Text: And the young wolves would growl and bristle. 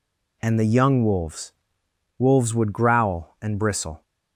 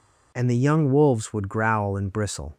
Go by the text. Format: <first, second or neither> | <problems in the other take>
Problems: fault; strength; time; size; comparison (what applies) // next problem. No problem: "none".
second | says "wolves" twice; at 2.1 s